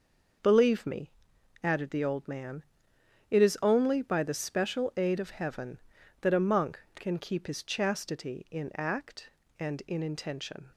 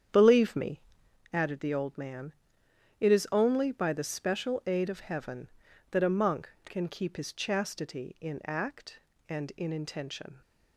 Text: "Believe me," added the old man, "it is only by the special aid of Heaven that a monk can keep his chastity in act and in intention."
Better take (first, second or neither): first